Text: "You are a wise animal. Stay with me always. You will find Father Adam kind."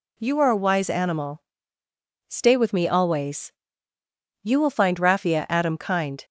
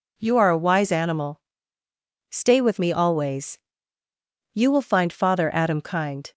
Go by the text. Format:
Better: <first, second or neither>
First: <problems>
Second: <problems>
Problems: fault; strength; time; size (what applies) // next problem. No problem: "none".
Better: second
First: says "Raffia" for "Father"; at 4.9 s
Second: none